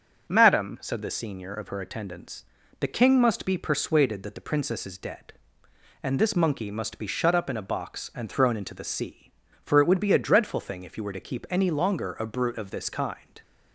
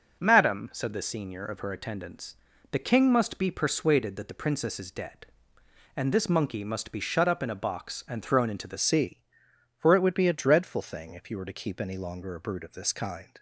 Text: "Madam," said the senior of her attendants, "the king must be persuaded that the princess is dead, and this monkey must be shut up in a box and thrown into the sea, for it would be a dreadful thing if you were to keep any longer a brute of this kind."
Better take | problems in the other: first | starts louder than the rest; until 1.2 s; 6.5 dB; also in the first // changes voice at "sea"; from 8.7 s on; 4.6 s long

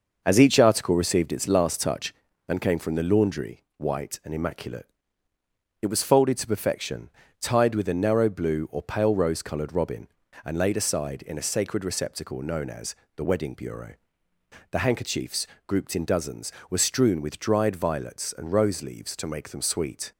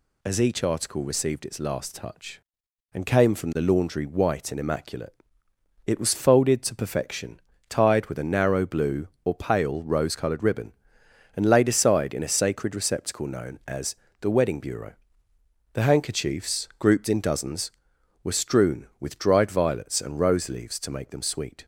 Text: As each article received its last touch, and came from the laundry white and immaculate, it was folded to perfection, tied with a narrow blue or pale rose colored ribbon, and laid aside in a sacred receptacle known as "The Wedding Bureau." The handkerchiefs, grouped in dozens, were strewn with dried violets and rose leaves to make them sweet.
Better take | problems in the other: second | says "robin" for "ribbon"; at 9.7 s // pauses between "as" and "The"; slight; at 12.9 s; 0.22 s long; slight in the second

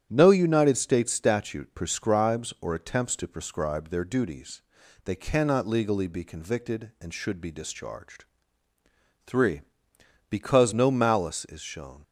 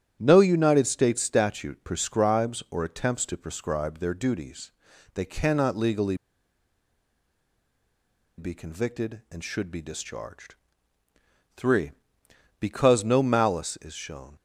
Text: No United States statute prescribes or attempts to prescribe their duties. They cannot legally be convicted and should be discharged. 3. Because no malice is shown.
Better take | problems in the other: first | starts louder than the rest; strong; until 1.2 s; 10 dB; strong in the first // pauses between "legally" and "be"; strong; at 6.1 s; 2.2 s long

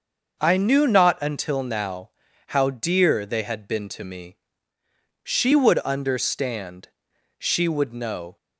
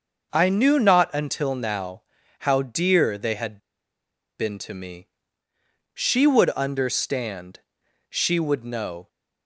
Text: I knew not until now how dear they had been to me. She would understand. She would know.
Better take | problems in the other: first | starts louder than the rest; until 1.3 s; 6 dB; also in the first // pauses between "now" and "how"; at 2.0 s; 0.38 s long; also in the first // pauses between "had" and "been"; noticeable; at 3.5 s; 0.80 s long

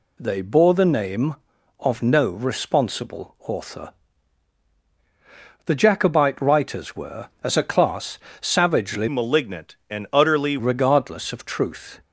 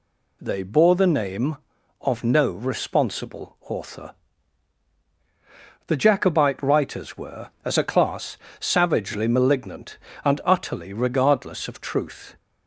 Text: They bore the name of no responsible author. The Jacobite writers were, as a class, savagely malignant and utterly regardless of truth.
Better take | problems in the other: second | changes voice from "malignant" to "utterly"; from 9.0 to 10.5 s; 1.5 s long

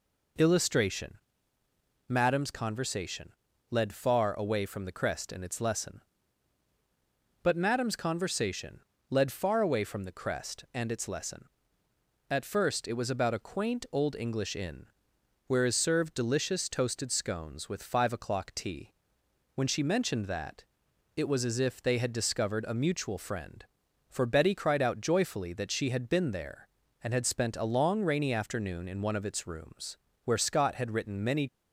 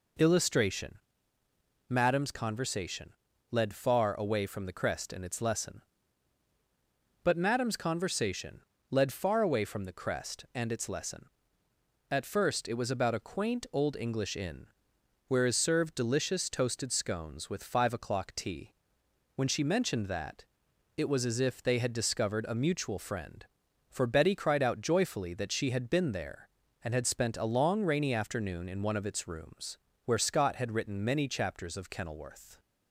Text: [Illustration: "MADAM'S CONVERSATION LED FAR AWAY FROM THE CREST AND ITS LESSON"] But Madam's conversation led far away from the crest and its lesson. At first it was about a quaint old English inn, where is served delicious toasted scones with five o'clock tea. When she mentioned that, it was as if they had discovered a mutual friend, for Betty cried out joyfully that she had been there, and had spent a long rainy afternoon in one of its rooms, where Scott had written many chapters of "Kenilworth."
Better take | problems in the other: second | pauses between "CONVERSATION" and "LED"; at 3.3 s; 0.38 s long; also in the second // pauses between "conversation" and "led"; slight; at 8.8 s; 0.28 s long; slight in the second // stops before "chapters of Kenilworth"; at 31.4 s

